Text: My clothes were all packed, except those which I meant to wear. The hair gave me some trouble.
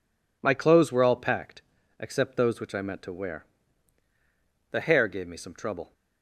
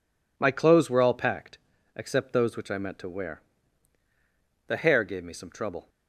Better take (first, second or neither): neither